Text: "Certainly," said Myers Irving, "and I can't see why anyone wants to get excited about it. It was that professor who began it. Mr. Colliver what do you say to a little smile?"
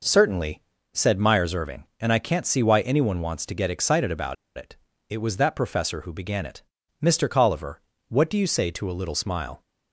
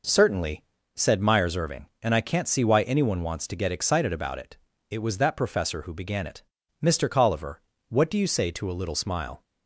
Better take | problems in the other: second | pauses between "about" and "it"; slight; at 4.3 s; 0.20 s long // pauses between "Colliver" and "what"; slight; at 7.8 s; 0.26 s long; slight in the second

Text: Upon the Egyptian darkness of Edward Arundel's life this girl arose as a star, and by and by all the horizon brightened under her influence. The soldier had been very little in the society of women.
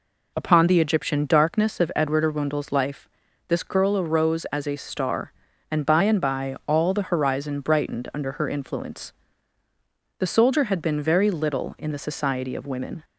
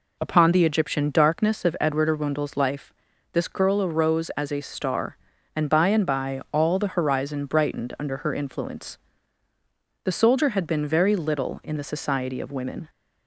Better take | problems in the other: neither | pauses between "life" and "this"; the same in both

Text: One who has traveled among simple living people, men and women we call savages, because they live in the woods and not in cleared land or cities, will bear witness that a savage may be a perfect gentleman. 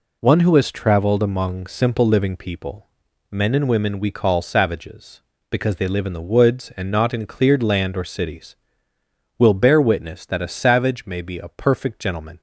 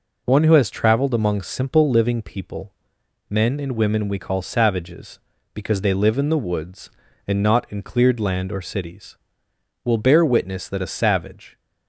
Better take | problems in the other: first | stops before "may be a perfect gentleman"; at 11.5 s

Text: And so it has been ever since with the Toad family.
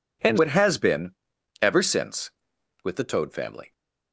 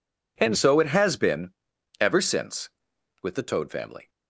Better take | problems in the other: second | skips "so"; at 0.3 s // pauses between "been" and "ever"; noticeable; at 1.1 s; 0.48 s long; noticeable in the second

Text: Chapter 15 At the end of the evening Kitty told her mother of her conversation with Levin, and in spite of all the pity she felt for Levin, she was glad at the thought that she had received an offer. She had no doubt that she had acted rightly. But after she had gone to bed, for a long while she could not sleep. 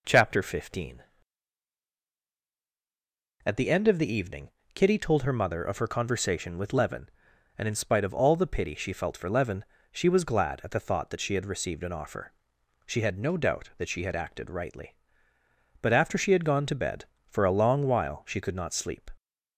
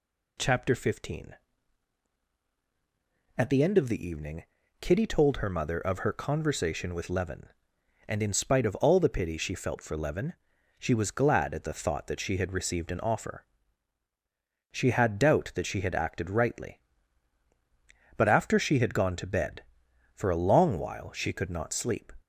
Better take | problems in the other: first | pauses between "evening" and "Kitty"; slight; at 4.4 s; 0.36 s long; slight in the first // skips "no"; at 15.1 s

